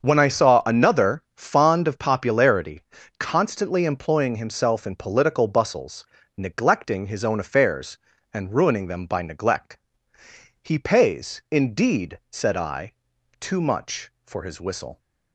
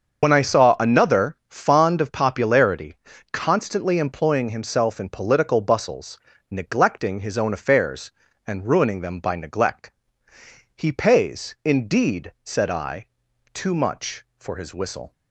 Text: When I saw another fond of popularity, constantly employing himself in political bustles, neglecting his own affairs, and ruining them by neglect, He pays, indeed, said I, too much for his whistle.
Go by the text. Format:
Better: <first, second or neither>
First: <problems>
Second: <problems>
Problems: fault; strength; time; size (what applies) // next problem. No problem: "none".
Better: first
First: starts louder than the rest; until 1.0 s; 6.5 dB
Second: loses the start of "When"; at 0.2 s; 70 ms // starts louder than the rest; until 1.2 s; 6.5 dB